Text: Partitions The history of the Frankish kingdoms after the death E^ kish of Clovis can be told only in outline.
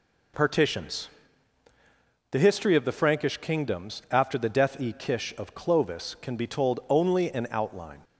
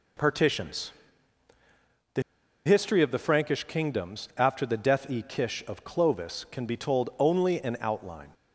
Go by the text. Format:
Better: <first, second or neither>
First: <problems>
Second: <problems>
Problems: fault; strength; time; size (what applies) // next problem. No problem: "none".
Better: first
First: pauses between "Partitions" and "The"; at 1.0 s; 1.2 s long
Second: pauses between "Partitions" and "The"; at 0.8 s; 1.2 s long // pauses between "The" and "history"; at 2.2 s; 0.43 s long